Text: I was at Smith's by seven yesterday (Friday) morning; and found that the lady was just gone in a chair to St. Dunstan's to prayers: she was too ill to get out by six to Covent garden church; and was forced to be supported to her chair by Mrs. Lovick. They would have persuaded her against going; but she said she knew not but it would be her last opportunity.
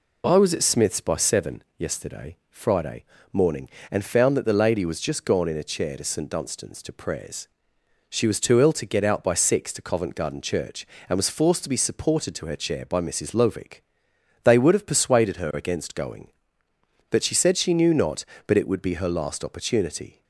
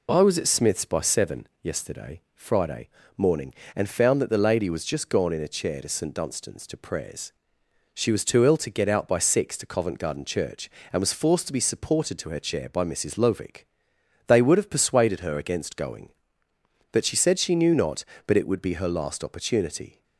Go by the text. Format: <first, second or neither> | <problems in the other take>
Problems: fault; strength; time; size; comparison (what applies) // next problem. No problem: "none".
neither | pauses between "seven" and "yesterday"; slight; the same in both